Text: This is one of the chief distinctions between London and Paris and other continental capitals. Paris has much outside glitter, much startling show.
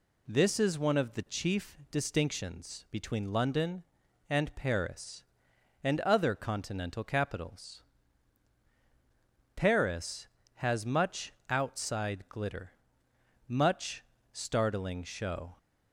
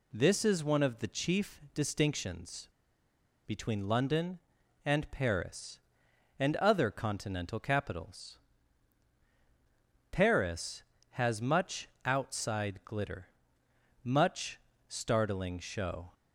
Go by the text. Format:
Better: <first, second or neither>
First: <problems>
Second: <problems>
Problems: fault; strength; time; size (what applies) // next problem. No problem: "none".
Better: first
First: pauses between "much" and "outside"; slight; at 11.3 s; 0.16 s long // pauses between "much" and "startling"; slight; at 14.0 s; 0.28 s long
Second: pauses between "distinctions" and "between"; noticeable; at 2.6 s; 0.76 s long // pauses between "much" and "outside"; slight; at 11.8 s; 0.16 s long // pauses between "much" and "startling"; slight; at 14.5 s; 0.28 s long